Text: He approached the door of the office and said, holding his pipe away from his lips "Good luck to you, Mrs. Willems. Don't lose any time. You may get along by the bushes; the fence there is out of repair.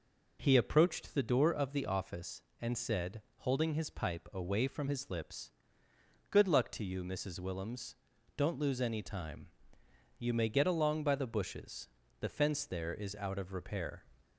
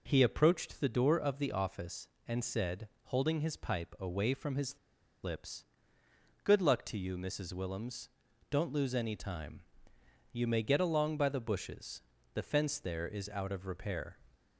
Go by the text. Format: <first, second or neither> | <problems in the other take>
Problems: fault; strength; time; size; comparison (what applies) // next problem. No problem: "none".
first | pauses between "his" and "lips"; at 4.7 s; 0.45 s long // pauses between "lips" and "Good"; noticeable; at 5.6 s; 0.80 s long; noticeable in the first